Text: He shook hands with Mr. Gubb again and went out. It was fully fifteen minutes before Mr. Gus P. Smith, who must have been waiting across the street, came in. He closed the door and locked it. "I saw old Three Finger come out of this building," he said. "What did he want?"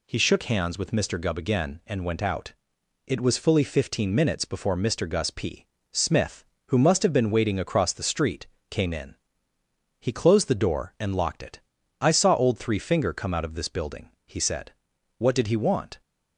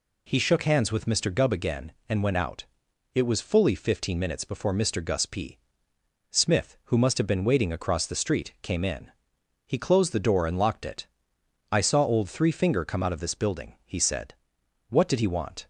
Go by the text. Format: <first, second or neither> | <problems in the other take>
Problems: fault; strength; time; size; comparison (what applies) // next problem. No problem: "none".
neither | none